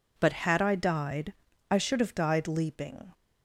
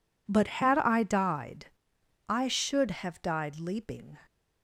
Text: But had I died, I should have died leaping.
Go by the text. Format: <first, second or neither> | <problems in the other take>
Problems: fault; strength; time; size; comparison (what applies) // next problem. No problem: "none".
neither | none